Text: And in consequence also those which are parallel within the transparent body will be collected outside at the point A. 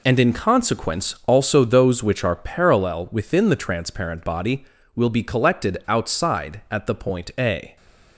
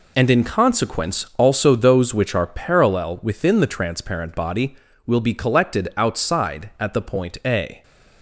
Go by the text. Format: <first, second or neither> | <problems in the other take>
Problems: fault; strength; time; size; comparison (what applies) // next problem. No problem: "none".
neither | none